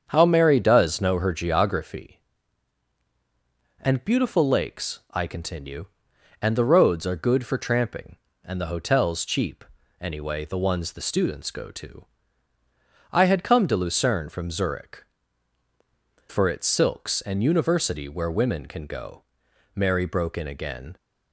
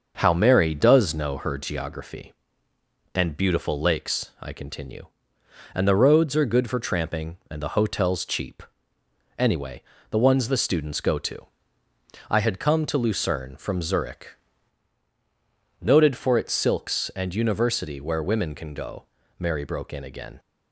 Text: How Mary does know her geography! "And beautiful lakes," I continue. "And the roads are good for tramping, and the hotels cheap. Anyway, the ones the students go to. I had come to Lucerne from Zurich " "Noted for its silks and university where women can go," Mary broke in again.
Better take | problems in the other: second | starts louder than the rest; strong; until 1.0 s; 7 dB; also in the second // skips "Noted"; at 16.3 s

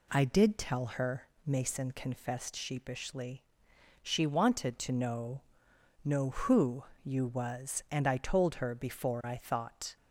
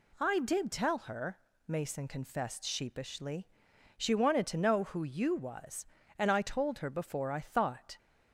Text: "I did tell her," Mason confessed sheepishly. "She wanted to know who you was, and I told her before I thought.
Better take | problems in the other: second | says "know" twice; at 6.0 s // pauses between "who" and "you"; slight; at 6.8 s; 0.20 s long

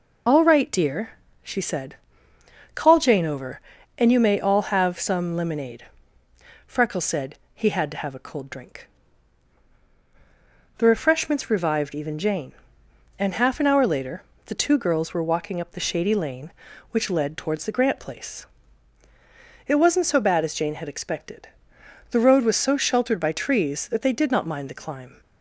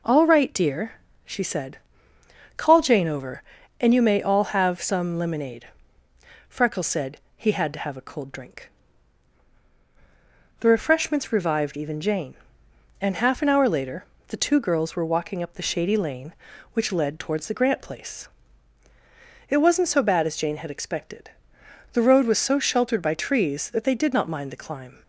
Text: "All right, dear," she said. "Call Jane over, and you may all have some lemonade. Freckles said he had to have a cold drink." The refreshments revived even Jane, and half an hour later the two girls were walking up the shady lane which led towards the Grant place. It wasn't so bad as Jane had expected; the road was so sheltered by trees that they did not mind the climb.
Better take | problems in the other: second | loses the start of "All"; at 0.2 s; 40 ms // pauses between "said" and "he"; slight; at 7.3 s; 0.18 s long; slight in the second // pauses between "later" and "the"; slight; at 14.2 s; 0.24 s long; slight in the second

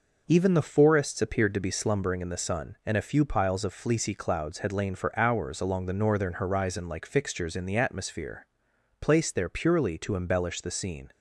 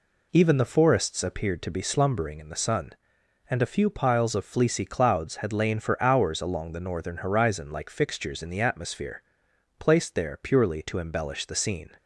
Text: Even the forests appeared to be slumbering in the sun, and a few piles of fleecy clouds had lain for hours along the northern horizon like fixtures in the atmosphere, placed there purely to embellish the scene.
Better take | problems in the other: neither | none

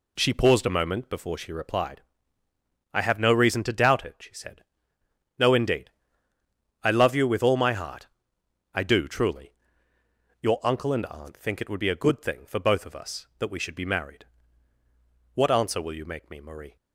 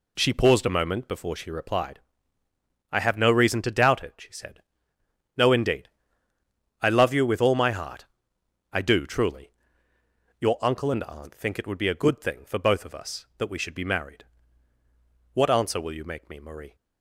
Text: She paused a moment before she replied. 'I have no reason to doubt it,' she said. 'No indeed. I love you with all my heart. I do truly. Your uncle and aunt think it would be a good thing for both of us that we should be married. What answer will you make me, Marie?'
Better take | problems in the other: neither | none

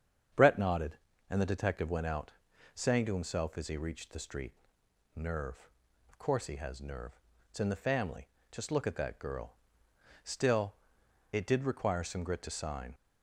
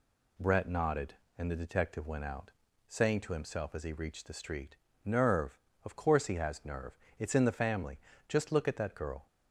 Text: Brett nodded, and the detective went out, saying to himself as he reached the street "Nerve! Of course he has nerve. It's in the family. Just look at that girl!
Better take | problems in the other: second | starts louder than the rest; strong; until 1.6 s; 7.5 dB // pauses between "street" and "Nerve"; noticeable; at 4.5 s; 0.62 s long; slight in the second // goes on to say "Still it did require some grit to sign"; strong; from 10.2 s on; 2.7 s long

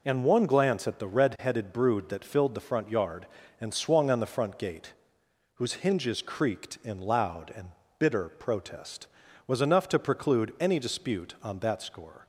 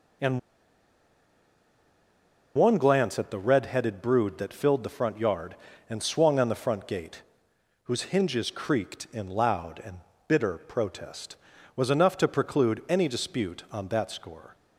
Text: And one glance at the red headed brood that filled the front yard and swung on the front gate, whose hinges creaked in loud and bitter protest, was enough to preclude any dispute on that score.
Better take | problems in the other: first | pauses between "And" and "one"; strong; at 0.3 s; 2.1 s long // pauses between "and" and "bitter"; slight; at 9.9 s; 0.30 s long; slight in the first

